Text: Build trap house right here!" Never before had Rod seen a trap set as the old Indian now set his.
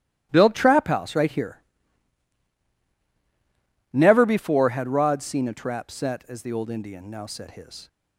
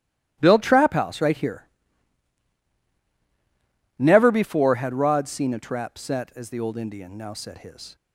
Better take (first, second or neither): neither